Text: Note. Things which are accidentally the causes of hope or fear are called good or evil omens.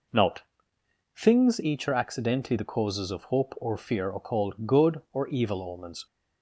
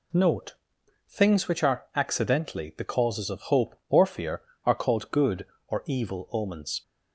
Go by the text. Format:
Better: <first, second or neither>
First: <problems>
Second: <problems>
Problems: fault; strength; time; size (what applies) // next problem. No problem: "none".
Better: second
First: says "each" for "which"; at 1.6 s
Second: none